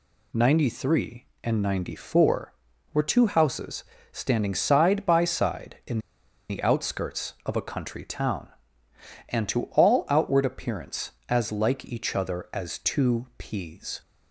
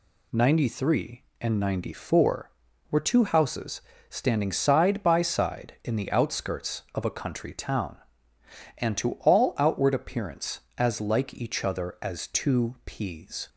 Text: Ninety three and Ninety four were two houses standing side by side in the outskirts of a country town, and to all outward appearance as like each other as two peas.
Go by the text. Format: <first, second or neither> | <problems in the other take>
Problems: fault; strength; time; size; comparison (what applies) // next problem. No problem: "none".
second | pauses between "houses" and "standing"; slight; at 3.8 s; 0.28 s long; slight in the second // pauses between "in" and "the"; noticeable; at 5.9 s; 0.51 s long